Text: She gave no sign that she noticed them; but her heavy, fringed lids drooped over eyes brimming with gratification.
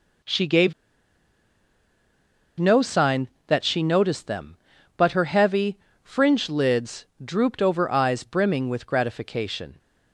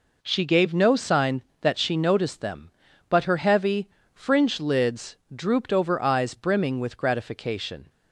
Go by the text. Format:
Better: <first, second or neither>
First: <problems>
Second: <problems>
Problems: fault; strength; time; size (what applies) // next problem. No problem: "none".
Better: second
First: pauses between "gave" and "no"; strong; at 0.7 s; 1.8 s long // pauses between "lids" and "drooped"; slight; at 7.0 s; 0.18 s long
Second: pauses between "lids" and "drooped"; slight; at 5.1 s; 0.18 s long